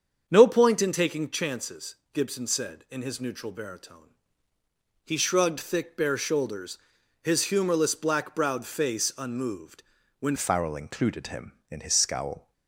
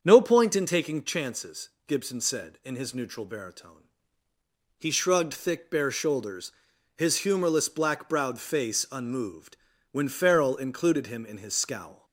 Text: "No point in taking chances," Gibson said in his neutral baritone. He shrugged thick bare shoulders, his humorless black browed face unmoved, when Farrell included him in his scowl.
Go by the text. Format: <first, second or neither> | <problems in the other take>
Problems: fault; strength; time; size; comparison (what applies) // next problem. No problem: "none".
second | starts louder than the rest; strong; until 1.2 s; 7 dB; strong in the second // changes voice at "Farrell"; from 10.3 s on; 2.2 s long